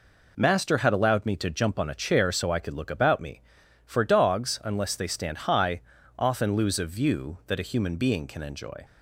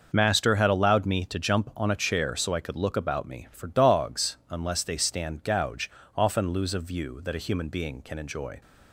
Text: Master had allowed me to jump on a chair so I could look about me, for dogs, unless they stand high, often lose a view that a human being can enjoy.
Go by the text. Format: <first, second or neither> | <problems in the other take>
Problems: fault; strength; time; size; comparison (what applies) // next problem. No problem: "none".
first | starts louder than the rest; noticeable; until 1.1 s; 6 dB // says "gouge" for "high"; at 5.4 s